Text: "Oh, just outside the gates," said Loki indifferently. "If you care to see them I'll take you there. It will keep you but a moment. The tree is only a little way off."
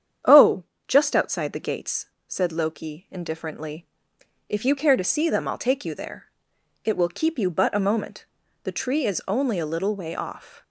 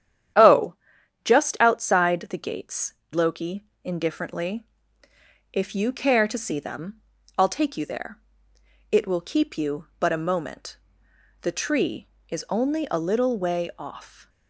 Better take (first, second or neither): first